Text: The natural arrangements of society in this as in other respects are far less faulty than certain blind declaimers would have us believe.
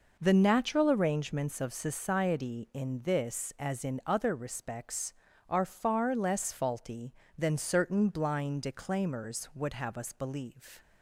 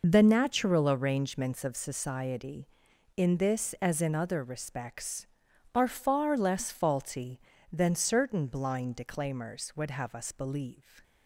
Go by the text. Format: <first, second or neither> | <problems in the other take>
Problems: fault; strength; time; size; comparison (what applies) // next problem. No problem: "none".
first | loses the start of "The"; at 0.0 s; 45 ms